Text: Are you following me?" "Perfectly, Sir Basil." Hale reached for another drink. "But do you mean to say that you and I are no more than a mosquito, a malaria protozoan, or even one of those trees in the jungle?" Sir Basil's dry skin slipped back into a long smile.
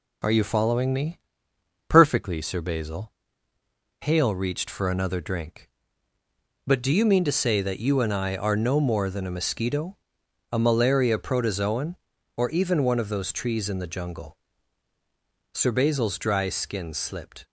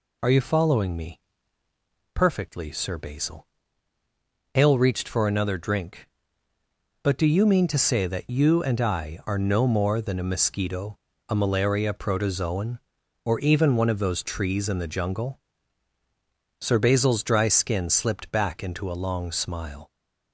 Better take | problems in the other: second | stops before "back into a long smile"; at 17.4 s

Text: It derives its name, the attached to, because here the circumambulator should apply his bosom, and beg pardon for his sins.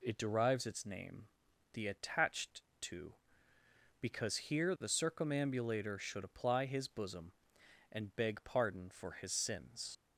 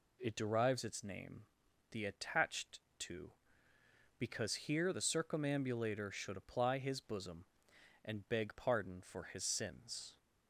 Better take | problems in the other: second | leaves "sins" unfinished; at 9.9 s; 110 ms

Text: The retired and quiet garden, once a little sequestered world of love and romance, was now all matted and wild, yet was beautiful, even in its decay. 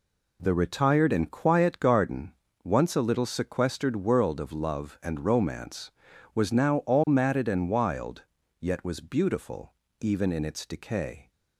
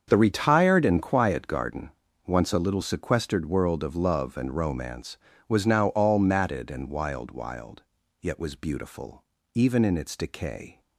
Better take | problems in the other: first | starts louder than the rest; until 1.0 s; 7 dB // says "wild" twice; at 7.3 s

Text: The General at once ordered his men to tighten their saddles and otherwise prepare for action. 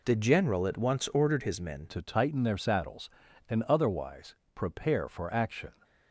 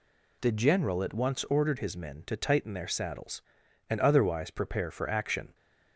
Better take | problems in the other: second | changes voice at "to"; from 1.8 s on; 3.9 s long // pauses between "otherwise" and "prepare"; slight; at 4.3 s; 0.22 s long

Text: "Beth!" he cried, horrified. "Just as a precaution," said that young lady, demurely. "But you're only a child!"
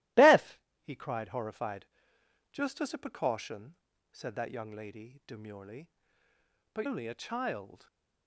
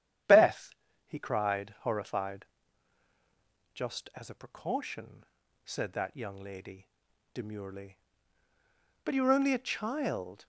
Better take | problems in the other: second | starts louder than the rest; strong; until 1.4 s; 16.5 dB; strong in the second // skips "you're"; at 6.8 s

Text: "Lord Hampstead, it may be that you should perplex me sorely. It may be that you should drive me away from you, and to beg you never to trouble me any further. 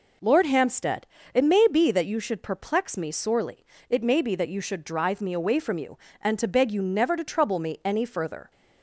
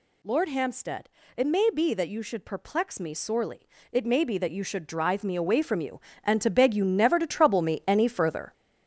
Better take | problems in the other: first | gets louder; throughout; 6.5 dB

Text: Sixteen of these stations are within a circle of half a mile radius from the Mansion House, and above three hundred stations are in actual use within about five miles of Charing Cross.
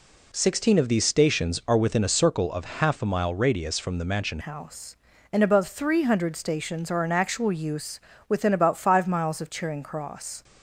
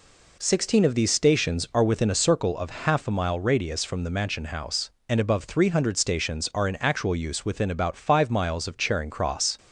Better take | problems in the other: second | changes voice at "House"; from 4.3 s on; 6.1 s long // pauses between "use" and "within"; slight; at 7.9 s; 0.30 s long

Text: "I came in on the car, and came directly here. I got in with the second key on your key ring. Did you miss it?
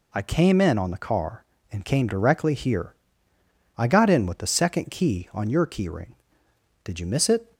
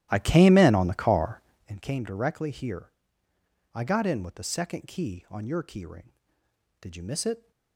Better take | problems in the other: first | starts louder than the rest; strong; until 1.8 s; 13.5 dB

